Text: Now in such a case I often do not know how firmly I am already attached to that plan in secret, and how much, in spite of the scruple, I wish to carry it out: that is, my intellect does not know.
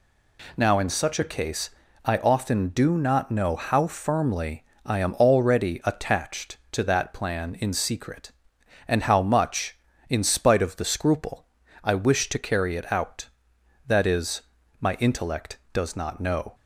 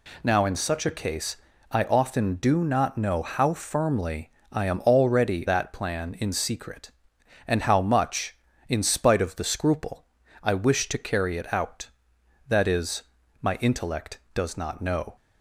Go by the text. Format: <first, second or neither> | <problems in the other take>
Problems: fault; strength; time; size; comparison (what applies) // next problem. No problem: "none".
first | pauses between "case" and "I"; slight; at 1.3 s; 0.34 s long; slight in the first // pauses between "firmly" and "I"; slight; at 4.3 s; 0.20 s long; slight in the first // skips "attached to"; at 5.4 s